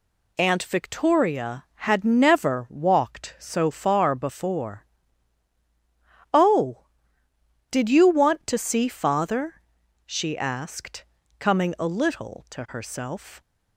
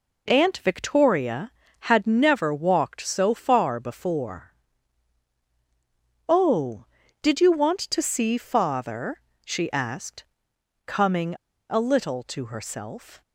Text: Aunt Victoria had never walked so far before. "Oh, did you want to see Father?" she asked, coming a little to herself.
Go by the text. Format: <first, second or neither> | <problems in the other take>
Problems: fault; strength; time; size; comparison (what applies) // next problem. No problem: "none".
first | pauses between "coming" and "a"; at 11.3 s; 0.38 s long